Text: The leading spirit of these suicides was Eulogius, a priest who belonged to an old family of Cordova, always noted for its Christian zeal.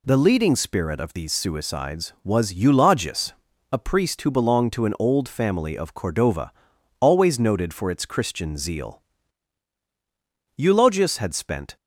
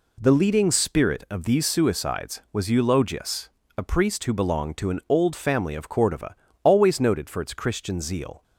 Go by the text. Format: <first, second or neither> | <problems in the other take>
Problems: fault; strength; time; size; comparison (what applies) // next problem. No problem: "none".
second | goes on to say "Eulogius had spent"; noticeable; from 10.5 s on; 1.1 s long